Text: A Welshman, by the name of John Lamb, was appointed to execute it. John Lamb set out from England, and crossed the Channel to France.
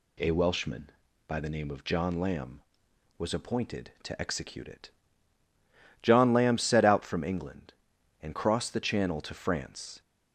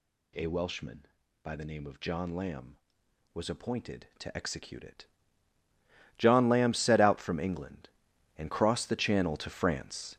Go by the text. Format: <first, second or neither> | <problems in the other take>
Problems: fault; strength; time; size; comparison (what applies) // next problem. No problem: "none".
first | gets louder; strong; throughout; 8.5 dB